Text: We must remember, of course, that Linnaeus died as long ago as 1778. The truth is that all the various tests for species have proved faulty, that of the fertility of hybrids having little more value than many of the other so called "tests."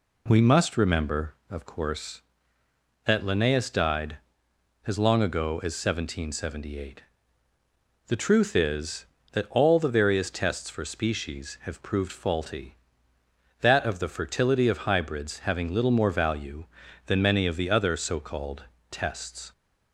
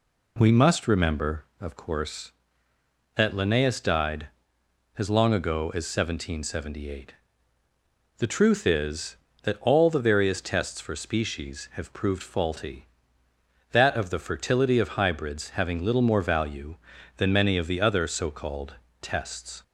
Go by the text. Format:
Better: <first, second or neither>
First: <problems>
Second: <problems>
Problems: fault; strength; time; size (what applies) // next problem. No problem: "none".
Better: neither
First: pauses between "called" and "tests"; slight; at 18.6 s; 0.26 s long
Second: pauses between "called" and "tests"; slight; at 18.7 s; 0.26 s long